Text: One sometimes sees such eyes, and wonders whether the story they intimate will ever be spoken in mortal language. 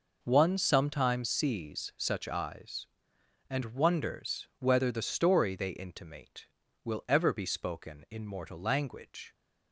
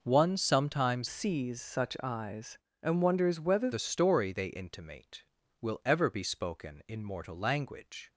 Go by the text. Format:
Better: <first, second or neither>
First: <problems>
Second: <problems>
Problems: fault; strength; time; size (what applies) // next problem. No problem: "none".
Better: first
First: none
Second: changes voice from "sees" to "whether"; from 1.0 to 3.7 s; 2.7 s long